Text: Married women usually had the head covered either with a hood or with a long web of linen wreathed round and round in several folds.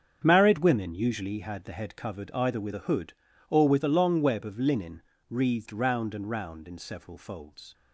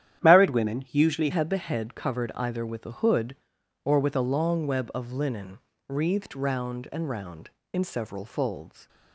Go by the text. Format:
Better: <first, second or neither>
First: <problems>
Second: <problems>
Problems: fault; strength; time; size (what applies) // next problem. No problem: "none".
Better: first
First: starts louder than the rest; strong; until 1.2 s; 7.5 dB // pauses between "linen" and "wreathed"; slight; at 5.0 s; 0.30 s long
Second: starts louder than the rest; strong; until 1.2 s; 10.5 dB // changes voice at "had"; from 1.3 s on; 7.5 s long // pauses between "linen" and "wreathed"; slight; at 5.5 s; 0.30 s long